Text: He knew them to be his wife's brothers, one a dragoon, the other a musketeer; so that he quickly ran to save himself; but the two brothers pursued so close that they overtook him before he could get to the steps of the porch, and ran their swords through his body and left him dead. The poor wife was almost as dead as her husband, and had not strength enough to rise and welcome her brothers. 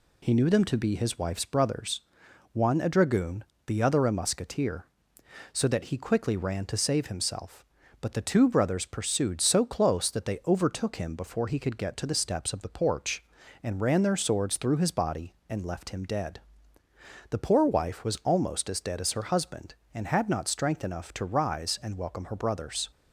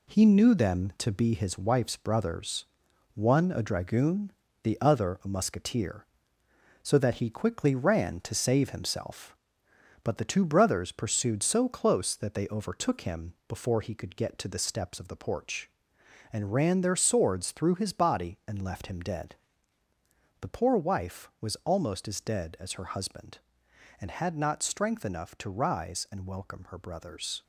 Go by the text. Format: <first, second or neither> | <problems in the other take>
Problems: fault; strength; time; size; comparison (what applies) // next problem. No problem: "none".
first | gets quieter; noticeable; throughout; 6 dB